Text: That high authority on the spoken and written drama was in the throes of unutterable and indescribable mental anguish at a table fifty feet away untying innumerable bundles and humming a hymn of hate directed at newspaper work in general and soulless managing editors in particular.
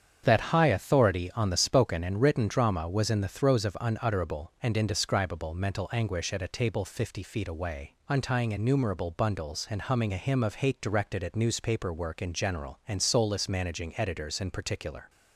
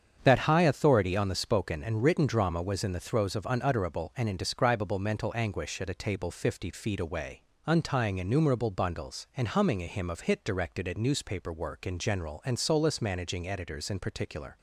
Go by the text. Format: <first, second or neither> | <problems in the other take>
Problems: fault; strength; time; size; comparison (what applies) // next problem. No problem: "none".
first | starts louder than the rest; strong; until 1.2 s; 7.5 dB; strong in the first // pauses between "away" and "untying"; slight; at 7.4 s; 0.26 s long; slight in the first // says "hit" for "hate"; at 10.2 s